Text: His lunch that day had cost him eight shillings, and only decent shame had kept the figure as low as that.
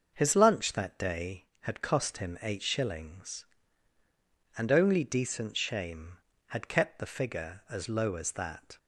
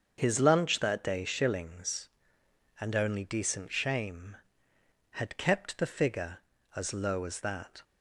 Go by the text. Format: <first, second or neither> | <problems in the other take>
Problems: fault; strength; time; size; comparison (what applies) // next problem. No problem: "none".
first | starts louder than the rest; until 1.1 s; 6.5 dB; also in the first // skips "had cost him eight"; at 1.2 s